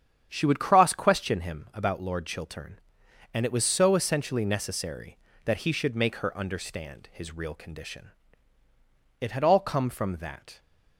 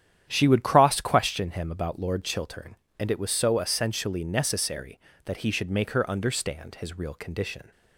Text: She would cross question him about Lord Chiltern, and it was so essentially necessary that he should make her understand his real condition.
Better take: second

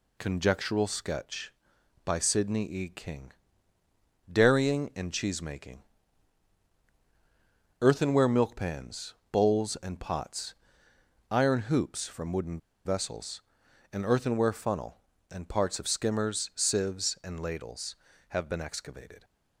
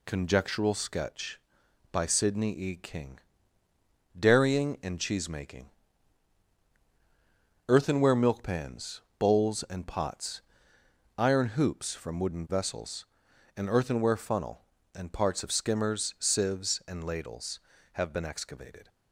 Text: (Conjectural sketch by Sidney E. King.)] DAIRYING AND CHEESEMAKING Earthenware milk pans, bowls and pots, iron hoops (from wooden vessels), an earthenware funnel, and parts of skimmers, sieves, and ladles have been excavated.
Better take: second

